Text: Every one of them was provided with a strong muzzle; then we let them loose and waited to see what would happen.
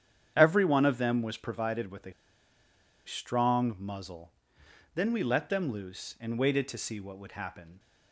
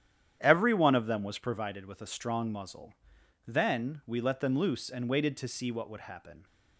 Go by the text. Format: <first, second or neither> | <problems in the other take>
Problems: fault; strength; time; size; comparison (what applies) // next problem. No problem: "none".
second | starts louder than the rest; strong; until 1.3 s; 9 dB; strong in the second // pauses between "a" and "strong"; noticeable; at 2.1 s; 0.94 s long